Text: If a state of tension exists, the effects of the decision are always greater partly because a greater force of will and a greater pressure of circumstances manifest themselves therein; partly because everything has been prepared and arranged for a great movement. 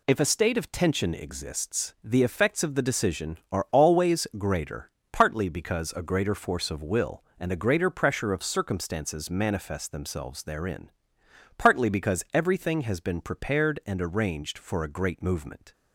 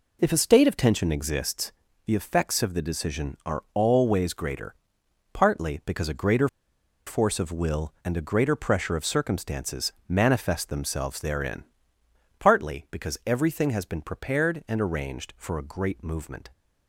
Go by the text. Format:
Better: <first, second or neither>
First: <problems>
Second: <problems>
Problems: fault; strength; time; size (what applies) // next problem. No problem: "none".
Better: first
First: pauses between "greater" and "partly"; slight; at 4.8 s; 0.22 s long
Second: pauses between "greater" and "partly"; noticeable; at 4.7 s; 0.58 s long // pauses between "greater" and "force"; noticeable; at 6.4 s; 0.58 s long